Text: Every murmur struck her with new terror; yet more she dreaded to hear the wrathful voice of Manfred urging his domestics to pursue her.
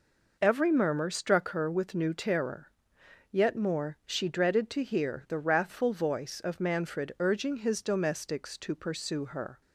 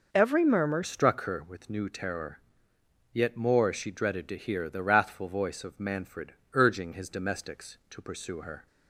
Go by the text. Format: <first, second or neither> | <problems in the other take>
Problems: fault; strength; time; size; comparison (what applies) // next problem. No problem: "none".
first | changes voice at "struck"; from 0.8 s on; 7.8 s long // pauses between "Manfred" and "urging"; slight; at 6.3 s; 0.18 s long